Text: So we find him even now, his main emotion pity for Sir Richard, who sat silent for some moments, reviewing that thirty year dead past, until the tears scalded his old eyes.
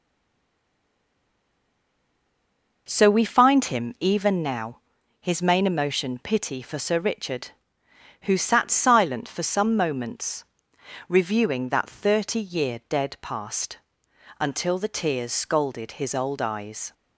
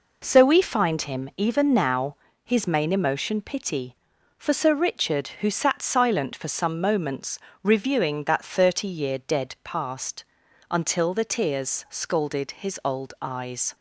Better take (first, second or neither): second